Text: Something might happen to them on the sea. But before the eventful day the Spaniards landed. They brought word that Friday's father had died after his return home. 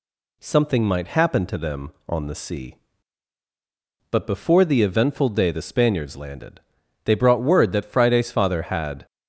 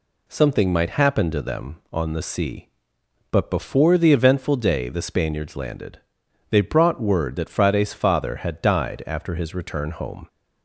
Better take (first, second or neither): second